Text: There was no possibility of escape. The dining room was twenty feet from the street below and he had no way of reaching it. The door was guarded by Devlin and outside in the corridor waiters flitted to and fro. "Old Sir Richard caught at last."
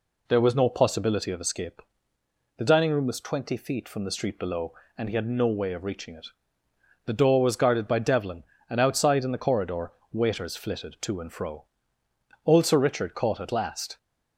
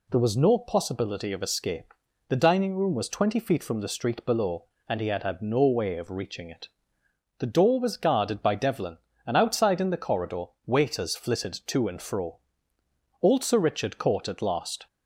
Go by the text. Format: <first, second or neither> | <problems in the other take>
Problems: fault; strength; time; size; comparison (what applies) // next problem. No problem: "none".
first | says "had" twice; at 5.2 s // pauses between "corridor" and "waiters"; slight; at 10.4 s; 0.20 s long; slight in the first